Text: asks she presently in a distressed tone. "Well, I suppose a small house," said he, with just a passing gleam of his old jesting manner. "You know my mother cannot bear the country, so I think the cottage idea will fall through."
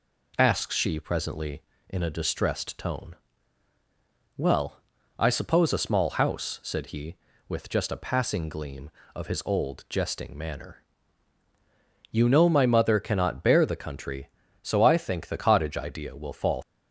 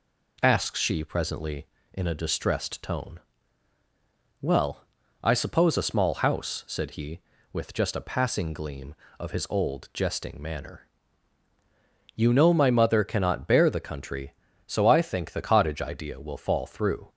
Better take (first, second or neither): second